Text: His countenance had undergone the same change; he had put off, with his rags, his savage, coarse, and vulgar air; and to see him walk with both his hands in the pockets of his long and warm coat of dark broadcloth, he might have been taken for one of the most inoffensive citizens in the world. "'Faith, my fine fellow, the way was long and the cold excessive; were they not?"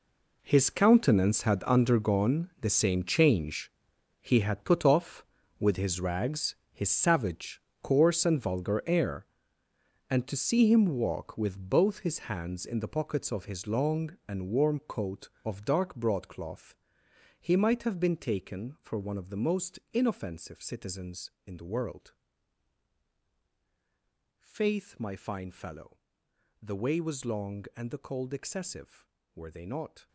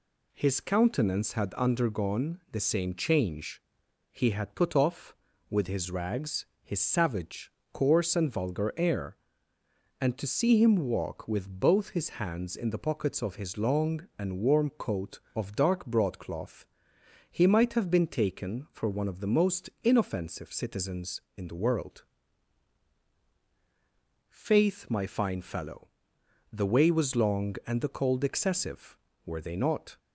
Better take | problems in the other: second | gets quieter; strong; throughout; 13.5 dB // pauses between "most" and "inoffensive"; slight; at 19.7 s; 0.16 s long; slight in the second

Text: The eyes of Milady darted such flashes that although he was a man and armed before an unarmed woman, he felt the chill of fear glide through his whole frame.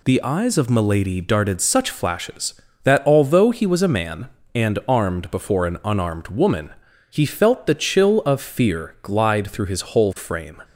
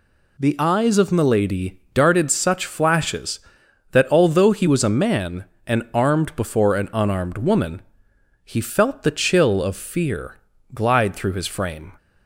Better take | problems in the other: first | pauses between "Milady" and "darted"; slight; at 1.7 s; 0.16 s long // pauses between "fear" and "glide"; slight; at 10.3 s; 0.34 s long // skips "whole"; at 11.4 s

